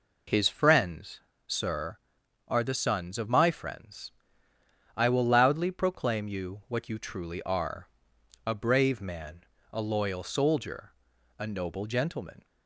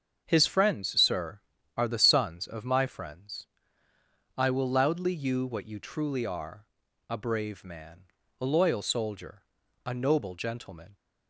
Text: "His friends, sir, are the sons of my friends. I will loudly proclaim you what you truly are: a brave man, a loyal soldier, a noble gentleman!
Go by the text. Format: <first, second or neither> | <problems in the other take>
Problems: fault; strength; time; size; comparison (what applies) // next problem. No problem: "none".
first | starts louder than the rest; until 1.2 s; 7 dB // skips "proclaim"; at 5.1 s